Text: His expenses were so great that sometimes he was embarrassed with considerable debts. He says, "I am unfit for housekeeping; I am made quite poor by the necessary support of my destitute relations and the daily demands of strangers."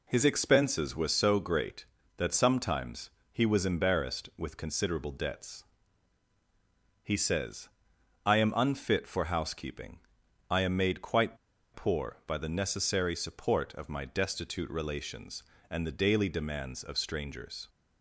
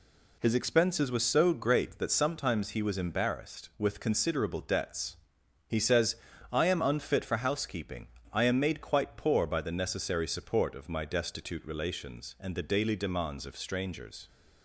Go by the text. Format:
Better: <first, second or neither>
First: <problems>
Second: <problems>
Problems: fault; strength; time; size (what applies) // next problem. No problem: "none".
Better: second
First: pauses between "sometimes" and "he"; slight; at 3.1 s; 0.20 s long // pauses between "quite" and "poor"; at 11.3 s; 0.37 s long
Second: none